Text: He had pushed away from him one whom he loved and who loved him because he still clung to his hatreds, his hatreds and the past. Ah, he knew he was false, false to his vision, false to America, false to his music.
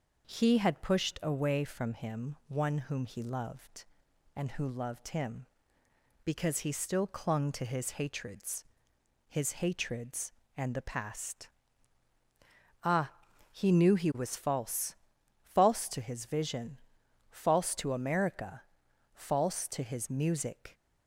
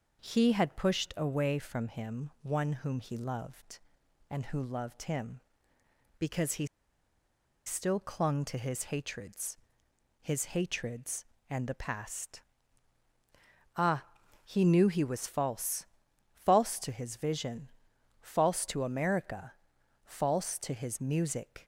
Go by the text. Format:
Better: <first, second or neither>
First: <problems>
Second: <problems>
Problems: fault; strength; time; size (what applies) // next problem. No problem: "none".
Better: first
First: none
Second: pauses between "he" and "still"; at 6.6 s; 1.0 s long